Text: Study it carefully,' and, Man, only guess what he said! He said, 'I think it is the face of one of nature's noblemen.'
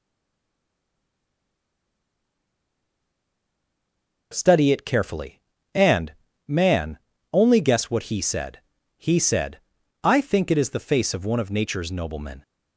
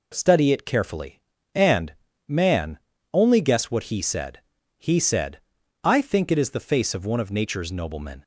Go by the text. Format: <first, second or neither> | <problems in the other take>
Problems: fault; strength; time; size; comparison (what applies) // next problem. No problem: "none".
second | stays silent before the first word; strong; until 4.3 s; 4.3 s long